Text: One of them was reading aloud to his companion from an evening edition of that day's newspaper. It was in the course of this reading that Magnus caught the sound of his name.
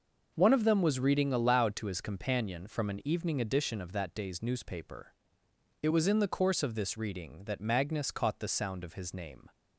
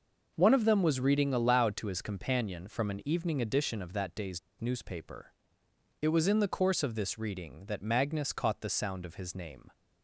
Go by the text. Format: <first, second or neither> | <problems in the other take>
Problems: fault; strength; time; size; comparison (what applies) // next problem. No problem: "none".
first | pauses between "day's" and "newspaper"; slight; at 4.3 s; 0.19 s long